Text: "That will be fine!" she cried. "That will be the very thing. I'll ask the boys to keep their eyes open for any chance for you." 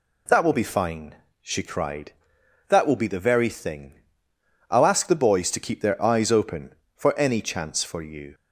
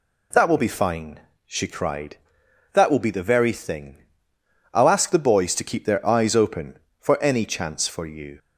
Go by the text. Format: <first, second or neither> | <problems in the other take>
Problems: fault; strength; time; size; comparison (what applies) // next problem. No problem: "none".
neither | none